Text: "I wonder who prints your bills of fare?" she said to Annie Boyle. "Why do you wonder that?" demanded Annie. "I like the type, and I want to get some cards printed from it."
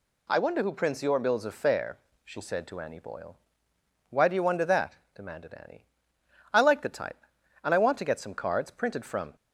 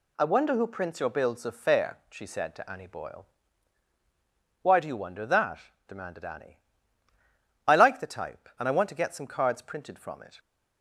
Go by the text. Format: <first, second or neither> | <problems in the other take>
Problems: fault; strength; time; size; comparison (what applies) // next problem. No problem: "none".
second | stops before "it"; at 9.3 s